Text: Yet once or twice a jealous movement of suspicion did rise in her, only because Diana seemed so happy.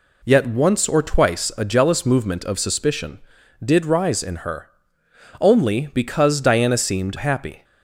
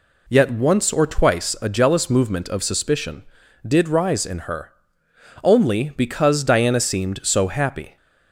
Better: second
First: skips "so"; at 7.1 s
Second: none

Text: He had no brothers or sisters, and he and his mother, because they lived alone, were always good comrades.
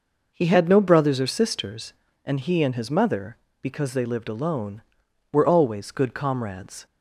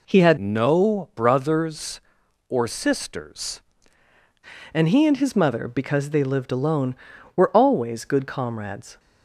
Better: first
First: none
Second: changes voice from "no" to "sisters"; from 0.3 to 3.6 s; 3.3 s long

